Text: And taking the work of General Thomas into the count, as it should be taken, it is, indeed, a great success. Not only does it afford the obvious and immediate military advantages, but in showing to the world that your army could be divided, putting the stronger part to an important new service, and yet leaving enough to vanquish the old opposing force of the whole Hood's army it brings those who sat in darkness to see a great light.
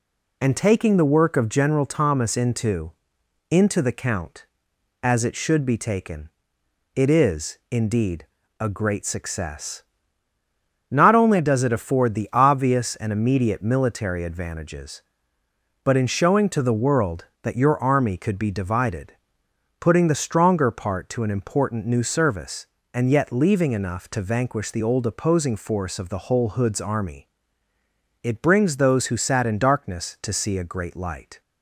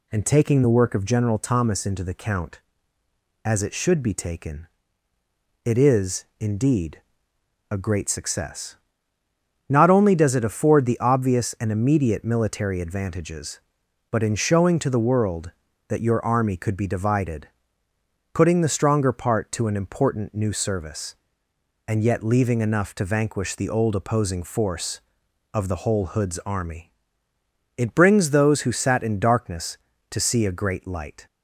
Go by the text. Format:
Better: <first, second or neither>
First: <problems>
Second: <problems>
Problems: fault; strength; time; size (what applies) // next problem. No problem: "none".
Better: second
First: says "into" twice; at 3.4 s // pauses between "army" and "it"; noticeable; at 27.2 s; 0.94 s long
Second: pauses between "army" and "it"; noticeable; at 26.9 s; 0.84 s long